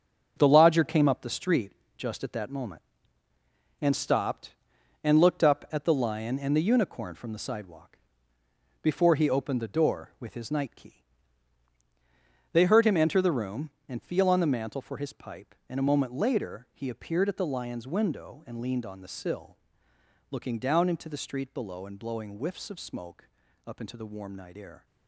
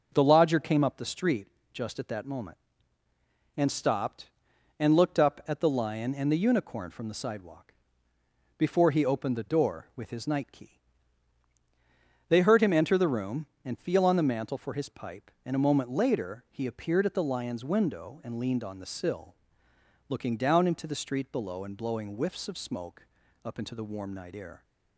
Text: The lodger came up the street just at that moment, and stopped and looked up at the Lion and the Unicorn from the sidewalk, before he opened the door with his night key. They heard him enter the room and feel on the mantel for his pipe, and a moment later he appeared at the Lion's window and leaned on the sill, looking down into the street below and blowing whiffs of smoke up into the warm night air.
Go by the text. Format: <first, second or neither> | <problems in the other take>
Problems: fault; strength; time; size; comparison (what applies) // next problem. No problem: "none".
second | gets quieter; strong; throughout; 8 dB // pauses between "street" and "just"; slight; at 1.7 s; 0.26 s long; slight in the second // pauses between "smoke" and "up"; at 23.2 s; 0.38 s long; also in the second